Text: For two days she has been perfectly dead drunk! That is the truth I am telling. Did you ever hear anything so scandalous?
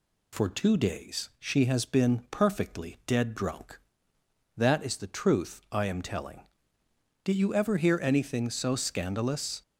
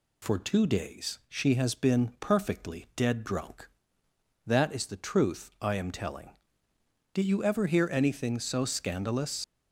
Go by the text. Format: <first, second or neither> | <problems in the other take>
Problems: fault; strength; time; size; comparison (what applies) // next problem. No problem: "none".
first | leaves "scandalous" unfinished; at 9.4 s; 70 ms